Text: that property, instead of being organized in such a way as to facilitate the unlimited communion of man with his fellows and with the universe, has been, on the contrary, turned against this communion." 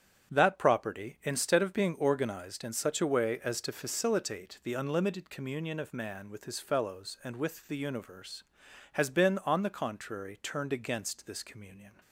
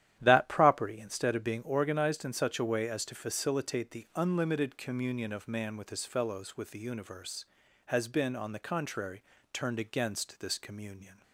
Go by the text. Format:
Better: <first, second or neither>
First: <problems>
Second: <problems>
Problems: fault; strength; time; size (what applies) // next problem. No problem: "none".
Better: first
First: starts louder than the rest; strong; until 1.3 s; 9 dB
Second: starts louder than the rest; strong; until 1.2 s; 11.5 dB // skips "and"; at 6.5 s